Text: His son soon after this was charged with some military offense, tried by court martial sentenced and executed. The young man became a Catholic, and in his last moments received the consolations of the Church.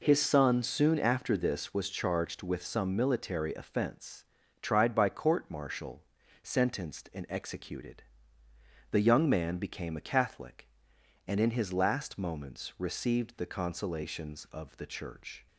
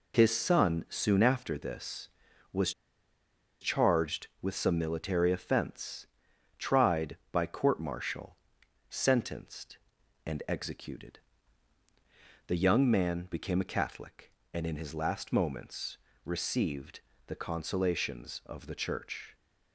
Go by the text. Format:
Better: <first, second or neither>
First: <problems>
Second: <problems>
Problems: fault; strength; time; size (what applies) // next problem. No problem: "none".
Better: first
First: pauses between "martial" and "sentenced"; at 6.0 s; 0.40 s long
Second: pauses between "was" and "charged"; noticeable; at 2.7 s; 0.89 s long // pauses between "martial" and "sentenced"; noticeable; at 8.3 s; 0.52 s long // pauses between "moments" and "received"; slight; at 15.9 s; 0.28 s long // pauses between "received" and "the"; slight; at 17.0 s; 0.26 s long